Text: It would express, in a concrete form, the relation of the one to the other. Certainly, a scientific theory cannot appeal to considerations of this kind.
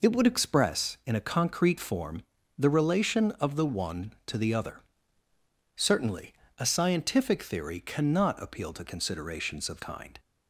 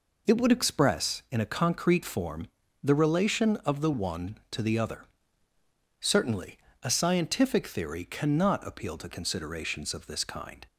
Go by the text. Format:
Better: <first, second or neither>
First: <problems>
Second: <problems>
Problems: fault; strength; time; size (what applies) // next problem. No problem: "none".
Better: second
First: skips "this"; at 9.8 s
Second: none